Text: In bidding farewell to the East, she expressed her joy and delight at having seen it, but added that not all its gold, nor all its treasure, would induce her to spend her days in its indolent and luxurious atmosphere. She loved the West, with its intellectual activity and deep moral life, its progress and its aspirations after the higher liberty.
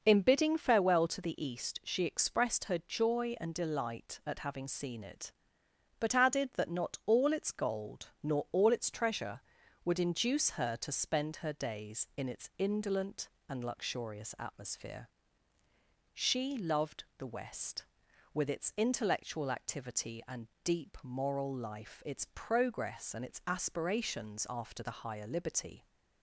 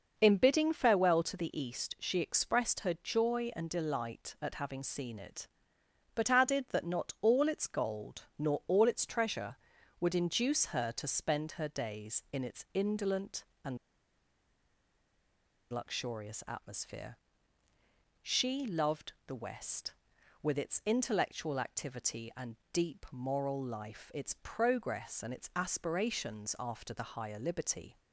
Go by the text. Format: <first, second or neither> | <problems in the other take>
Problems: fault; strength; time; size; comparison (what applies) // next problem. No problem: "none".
first | pauses between "and" and "luxurious"; strong; at 13.7 s; 1.9 s long // pauses between "loved" and "the"; slight; at 19.1 s; 0.16 s long; slight in the first // pauses between "and" and "deep"; slight; at 22.5 s; 0.18 s long; slight in the first